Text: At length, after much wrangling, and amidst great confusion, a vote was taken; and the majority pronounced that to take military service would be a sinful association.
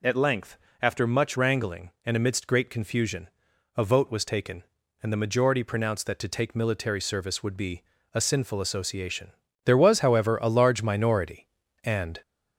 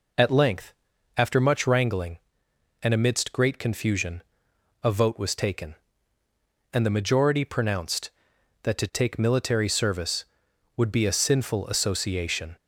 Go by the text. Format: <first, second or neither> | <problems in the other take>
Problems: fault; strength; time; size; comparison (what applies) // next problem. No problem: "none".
second | pauses between "be" and "a"; slight; at 7.8 s; 0.30 s long // goes on to say "There was however a large minority and"; strong; from 9.6 s on; 2.5 s long